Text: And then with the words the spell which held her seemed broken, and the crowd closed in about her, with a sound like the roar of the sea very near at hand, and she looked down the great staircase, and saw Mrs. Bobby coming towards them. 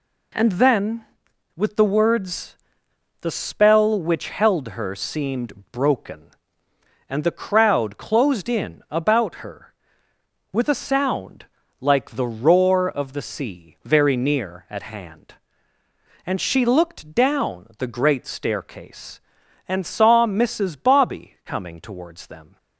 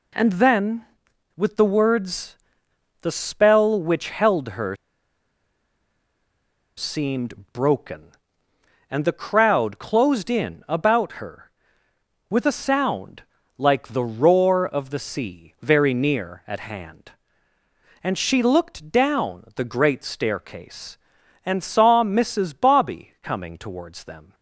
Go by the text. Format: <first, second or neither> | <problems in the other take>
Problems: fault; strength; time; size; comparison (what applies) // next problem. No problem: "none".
first | pauses between "words" and "the"; noticeable; at 2.3 s; 0.66 s long; noticeable in the first // pauses between "her" and "seemed"; strong; at 4.7 s; 2.0 s long // pauses between "seemed" and "broken"; slight; at 7.3 s; 0.18 s long; slight in the first // pauses between "sound" and "like"; slight; at 13.2 s; 0.36 s long; slight in the first